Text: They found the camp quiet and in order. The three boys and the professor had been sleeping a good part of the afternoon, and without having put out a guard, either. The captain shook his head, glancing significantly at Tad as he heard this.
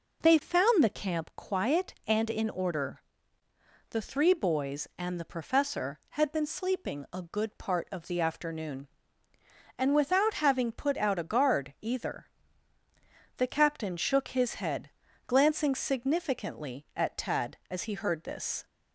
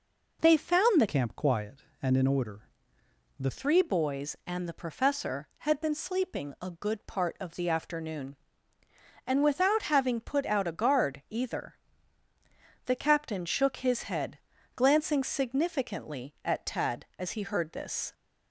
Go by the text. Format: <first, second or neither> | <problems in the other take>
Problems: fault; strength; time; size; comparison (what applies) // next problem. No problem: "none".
first | changes voice from "camp" to "The"; from 1.0 to 3.5 s; 2.5 s long